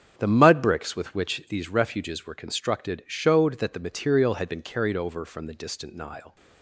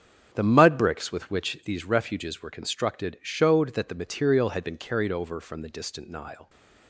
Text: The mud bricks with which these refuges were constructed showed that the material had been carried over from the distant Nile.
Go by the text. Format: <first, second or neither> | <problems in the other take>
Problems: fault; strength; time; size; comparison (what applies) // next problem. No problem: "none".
neither | starts louder than the rest; strong; the same in both